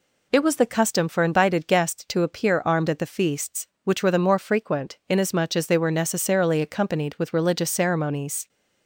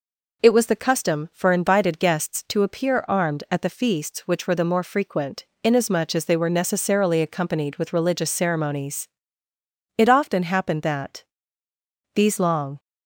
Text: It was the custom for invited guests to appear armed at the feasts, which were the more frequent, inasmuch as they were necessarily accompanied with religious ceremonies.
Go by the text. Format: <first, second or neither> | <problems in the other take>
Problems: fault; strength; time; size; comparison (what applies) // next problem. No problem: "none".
first | goes on to say "It often happened that these long"; strong; from 9.9 s on; 2.8 s long